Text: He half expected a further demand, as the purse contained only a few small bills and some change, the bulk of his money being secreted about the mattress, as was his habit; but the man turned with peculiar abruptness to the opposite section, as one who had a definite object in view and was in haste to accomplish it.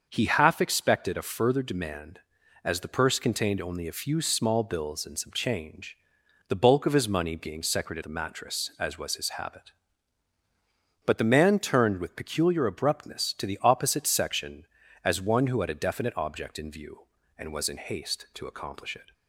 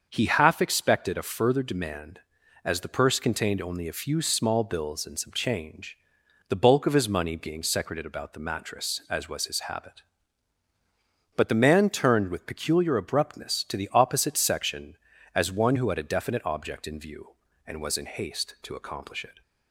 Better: second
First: starts louder than the rest; until 1.0 s; 6.5 dB // skips "about"; at 8.0 s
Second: starts louder than the rest; until 1.1 s; 6.5 dB

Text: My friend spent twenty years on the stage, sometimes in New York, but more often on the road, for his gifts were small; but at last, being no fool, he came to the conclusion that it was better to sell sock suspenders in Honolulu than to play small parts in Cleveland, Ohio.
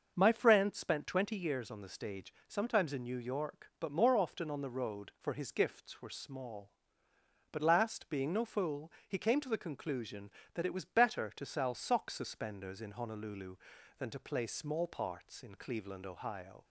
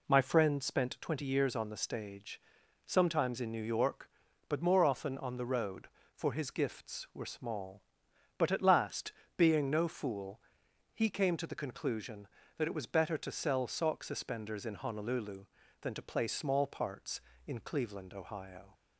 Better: second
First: starts louder than the rest; until 1.1 s; 6 dB // skips "at"; at 7.6 s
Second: none

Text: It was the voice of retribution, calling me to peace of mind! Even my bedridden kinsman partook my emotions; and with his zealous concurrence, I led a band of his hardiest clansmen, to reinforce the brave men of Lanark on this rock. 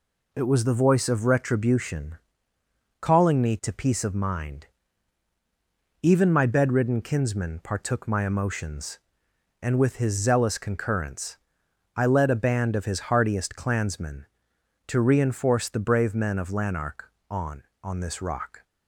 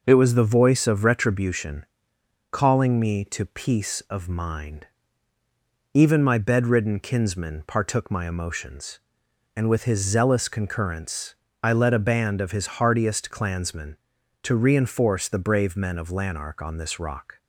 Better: second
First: says "on" twice; at 17.8 s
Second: none

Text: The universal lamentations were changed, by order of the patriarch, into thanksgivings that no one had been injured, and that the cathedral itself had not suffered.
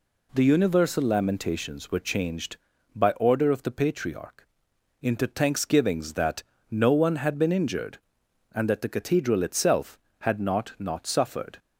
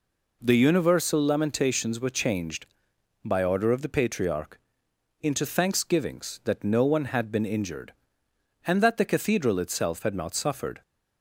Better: second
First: pauses between "that" and "no"; slight; at 6.4 s; 0.26 s long // says "not" twice; at 10.7 s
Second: none

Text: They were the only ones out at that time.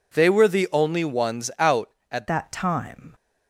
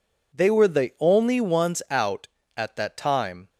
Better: second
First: changes voice at "that"; from 2.2 s on; 0.9 s long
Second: none

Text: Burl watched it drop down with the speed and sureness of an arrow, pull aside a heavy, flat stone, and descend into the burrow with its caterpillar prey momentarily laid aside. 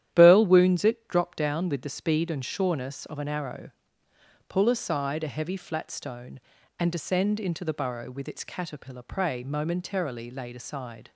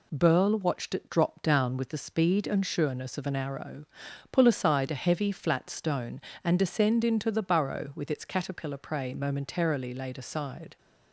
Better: second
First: starts louder than the rest; strong; until 1.1 s; 11 dB // says "wounds" for "watched"; at 0.4 s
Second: none

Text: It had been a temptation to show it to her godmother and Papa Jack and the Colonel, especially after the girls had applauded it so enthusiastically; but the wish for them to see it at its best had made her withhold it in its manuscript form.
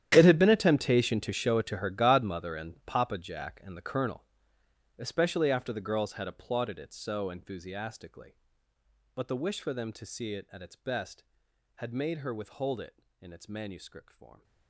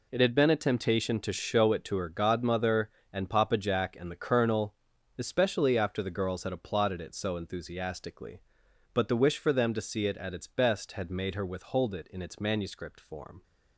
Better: second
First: gets quieter; strong; throughout; 19 dB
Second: none

